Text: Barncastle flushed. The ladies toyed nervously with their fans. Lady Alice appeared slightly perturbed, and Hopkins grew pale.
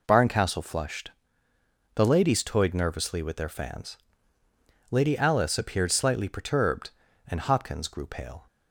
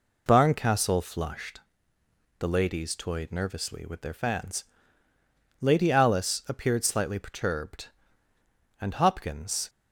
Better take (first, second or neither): first